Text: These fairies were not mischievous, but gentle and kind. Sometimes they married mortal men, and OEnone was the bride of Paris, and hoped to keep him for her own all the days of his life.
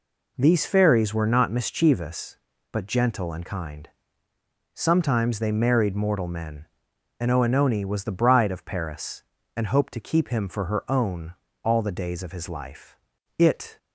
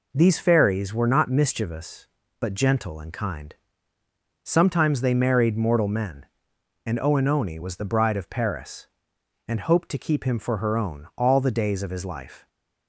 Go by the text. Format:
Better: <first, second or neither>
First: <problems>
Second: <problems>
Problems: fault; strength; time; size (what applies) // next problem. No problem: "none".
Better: second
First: pauses between "own" and "all"; slight; at 11.3 s; 0.30 s long // goes on to say "It"; slight; from 13.3 s on; 0.40 s long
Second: none